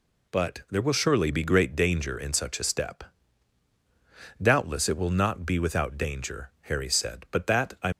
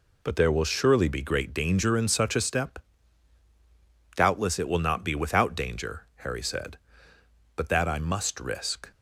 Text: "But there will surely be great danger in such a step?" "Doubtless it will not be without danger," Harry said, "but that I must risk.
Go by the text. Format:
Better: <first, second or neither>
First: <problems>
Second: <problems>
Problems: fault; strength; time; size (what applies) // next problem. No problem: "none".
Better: second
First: stops before "must risk"; at 7.9 s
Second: none